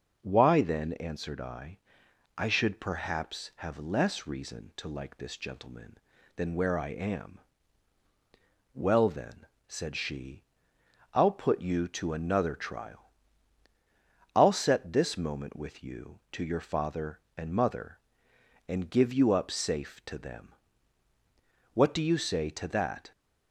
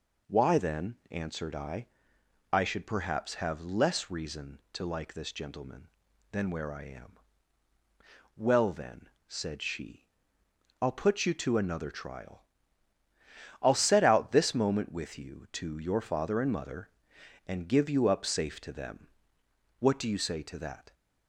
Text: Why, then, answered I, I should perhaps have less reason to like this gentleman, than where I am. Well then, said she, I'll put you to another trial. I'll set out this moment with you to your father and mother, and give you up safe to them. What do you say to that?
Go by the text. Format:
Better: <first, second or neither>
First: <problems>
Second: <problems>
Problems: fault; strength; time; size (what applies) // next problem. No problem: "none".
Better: second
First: skips "out"; at 14.9 s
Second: none